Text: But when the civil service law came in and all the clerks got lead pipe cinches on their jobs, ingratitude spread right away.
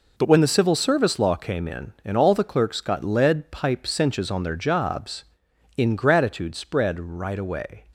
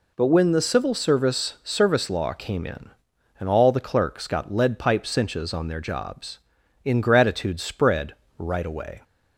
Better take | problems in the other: first | says "service" twice; at 1.6 s // pauses between "spread" and "right"; slight; at 8.1 s; 0.24 s long

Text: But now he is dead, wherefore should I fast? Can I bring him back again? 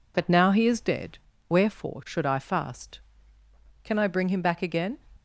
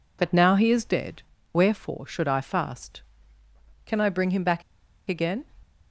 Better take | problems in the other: first | pauses between "back" and "again"; noticeable; at 4.6 s; 0.47 s long

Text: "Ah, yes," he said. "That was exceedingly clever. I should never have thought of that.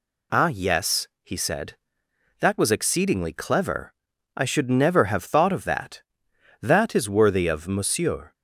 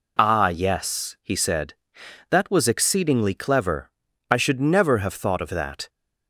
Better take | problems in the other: second | goes on to say "That is worthy of Monsieur"; strong; from 6.5 s on; 1.7 s long

